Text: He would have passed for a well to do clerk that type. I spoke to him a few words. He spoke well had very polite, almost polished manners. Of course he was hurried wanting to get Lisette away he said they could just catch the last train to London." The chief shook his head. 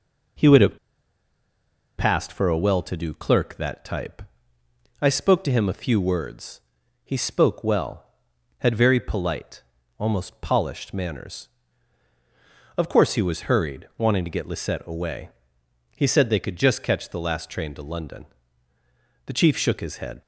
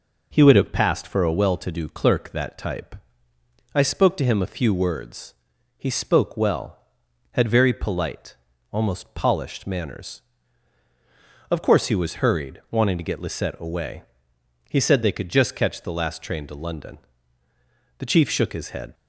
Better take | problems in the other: second | pauses between "have" and "passed"; at 0.7 s; 1.2 s long // pauses between "away" and "he"; noticeable; at 15.2 s; 0.66 s long; noticeable in the second

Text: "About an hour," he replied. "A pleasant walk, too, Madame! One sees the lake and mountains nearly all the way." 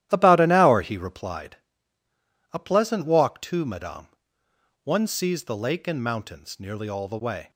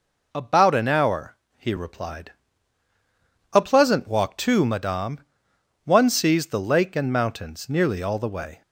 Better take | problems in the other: second | starts louder than the rest; strong; until 1.4 s; 12 dB

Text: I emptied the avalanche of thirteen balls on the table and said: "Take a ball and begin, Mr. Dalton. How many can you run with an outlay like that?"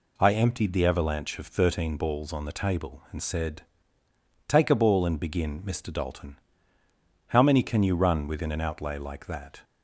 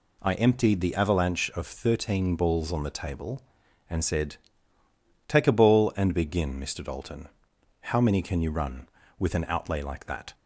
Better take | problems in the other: second | says "within" for "with"; at 8.2 s

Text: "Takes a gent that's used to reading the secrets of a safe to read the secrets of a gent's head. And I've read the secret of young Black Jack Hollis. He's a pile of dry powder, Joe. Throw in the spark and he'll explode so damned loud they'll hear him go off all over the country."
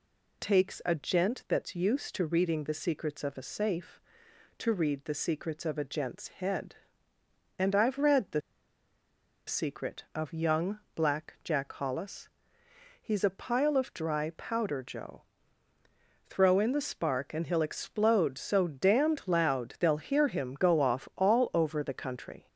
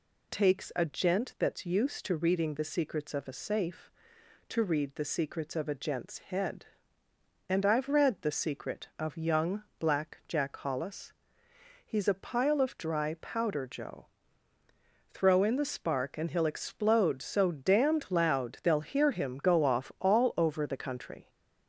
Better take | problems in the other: second | pauses between "the" and "secret"; at 8.4 s; 1.0 s long // pauses between "young" and "Black"; slight; at 10.7 s; 0.16 s long; slight in the second

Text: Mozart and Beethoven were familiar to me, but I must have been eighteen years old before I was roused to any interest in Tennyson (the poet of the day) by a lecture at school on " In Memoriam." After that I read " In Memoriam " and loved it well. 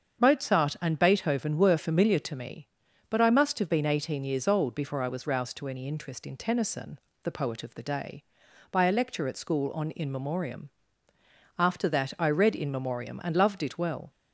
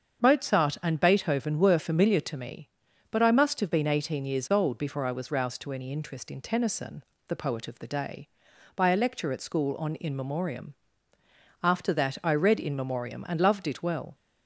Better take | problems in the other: neither | starts louder than the rest; strong; the same in both

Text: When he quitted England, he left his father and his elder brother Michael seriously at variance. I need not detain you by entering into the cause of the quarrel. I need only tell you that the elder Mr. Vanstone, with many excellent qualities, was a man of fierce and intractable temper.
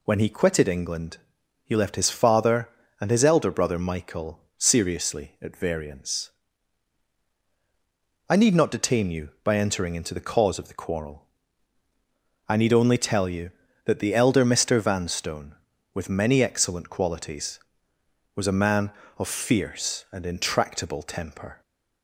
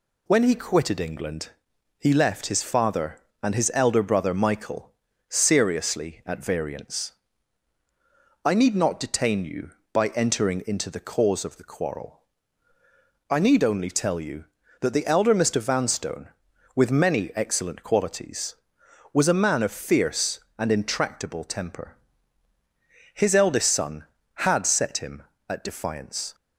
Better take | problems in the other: first | pauses between "Michael" and "seriously"; at 4.9 s; 0.38 s long; slight in the first // goes on to say "His eldest son had set him at defiance"; strong; from 23.1 s on; 3.2 s long

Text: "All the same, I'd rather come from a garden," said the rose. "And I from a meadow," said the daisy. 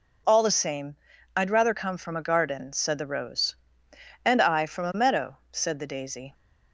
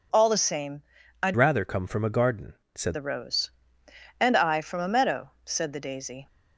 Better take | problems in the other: first | changes voice from "rather" to "said"; from 1.3 to 2.9 s; 1.6 s long

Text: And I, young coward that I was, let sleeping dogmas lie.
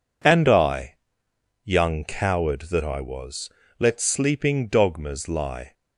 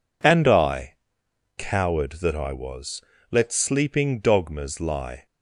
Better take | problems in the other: first | skips "young"; at 1.2 s

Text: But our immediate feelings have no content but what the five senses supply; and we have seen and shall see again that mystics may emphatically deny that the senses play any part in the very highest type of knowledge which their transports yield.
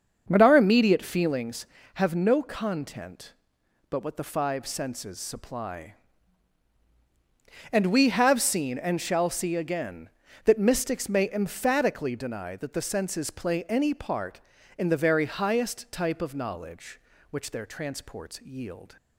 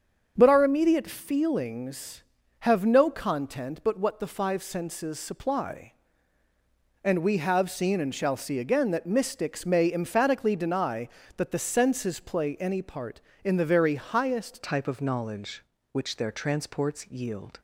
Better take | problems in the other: first | starts louder than the rest; until 1.3 s; 7 dB; also in the first // changes voice at "type"; from 14.6 s on; 3.0 s long

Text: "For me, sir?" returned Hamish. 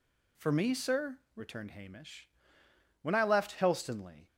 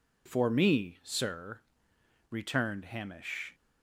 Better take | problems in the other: second | goes on to say "When I left Helstonleigh"; noticeable; from 3.0 s on; 1.2 s long

